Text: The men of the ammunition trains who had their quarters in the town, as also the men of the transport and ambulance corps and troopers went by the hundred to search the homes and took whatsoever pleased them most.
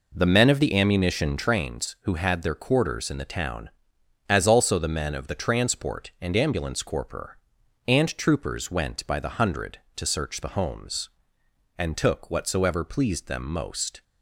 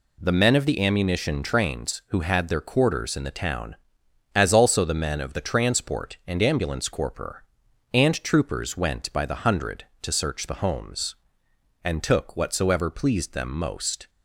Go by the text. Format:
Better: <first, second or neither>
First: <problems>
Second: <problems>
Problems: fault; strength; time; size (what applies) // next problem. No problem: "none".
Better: second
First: starts louder than the rest; noticeable; until 1.5 s; 4.5 dB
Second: none